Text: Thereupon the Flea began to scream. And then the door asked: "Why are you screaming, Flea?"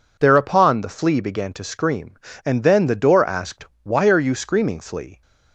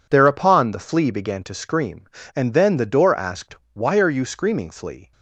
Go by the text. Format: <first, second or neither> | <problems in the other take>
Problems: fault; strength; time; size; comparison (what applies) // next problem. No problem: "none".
first | gets quieter; strong; throughout; 10 dB